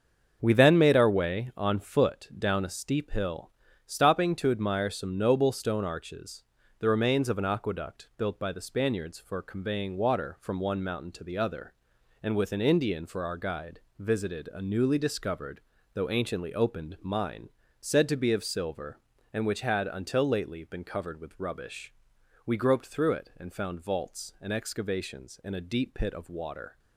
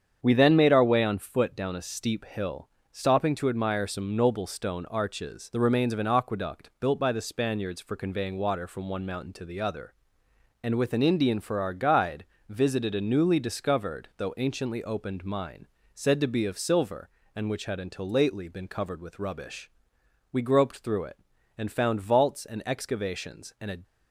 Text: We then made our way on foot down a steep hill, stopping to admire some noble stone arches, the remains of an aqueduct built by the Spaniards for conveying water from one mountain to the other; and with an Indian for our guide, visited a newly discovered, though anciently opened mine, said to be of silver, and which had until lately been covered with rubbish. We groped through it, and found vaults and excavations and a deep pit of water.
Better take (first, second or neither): first